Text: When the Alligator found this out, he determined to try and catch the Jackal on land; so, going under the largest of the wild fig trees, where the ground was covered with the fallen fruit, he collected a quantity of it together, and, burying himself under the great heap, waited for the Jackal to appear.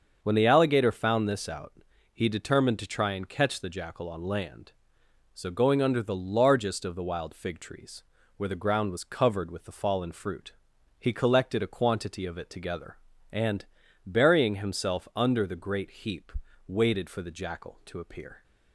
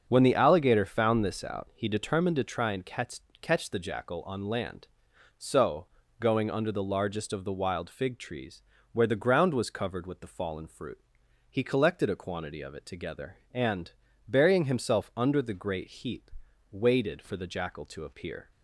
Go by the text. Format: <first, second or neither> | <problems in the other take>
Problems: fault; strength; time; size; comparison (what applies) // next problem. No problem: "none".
first | starts louder than the rest; until 1.1 s; 6.5 dB; also in the first // says "catch" twice; at 3.4 s